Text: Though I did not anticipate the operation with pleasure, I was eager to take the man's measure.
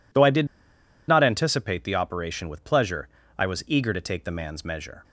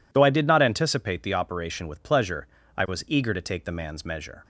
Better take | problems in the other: second | pauses between "did" and "not"; noticeable; at 0.4 s; 0.61 s long

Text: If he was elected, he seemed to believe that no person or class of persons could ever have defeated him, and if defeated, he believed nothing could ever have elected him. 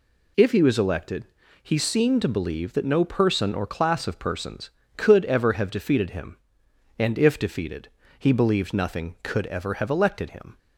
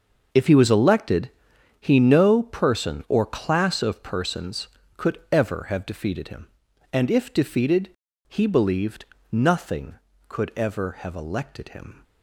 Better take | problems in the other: first | starts louder than the rest; noticeable; until 1.8 s; 6 dB // skips "seemed to believe that"; at 1.9 s // pauses between "believed" and "nothing"; slight; at 9.0 s; 0.26 s long

